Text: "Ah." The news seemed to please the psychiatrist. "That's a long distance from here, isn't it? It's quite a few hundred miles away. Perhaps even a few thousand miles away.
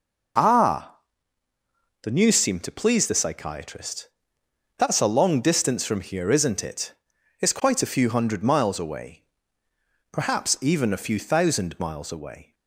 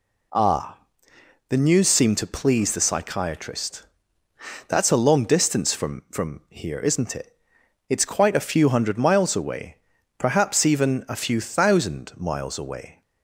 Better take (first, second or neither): first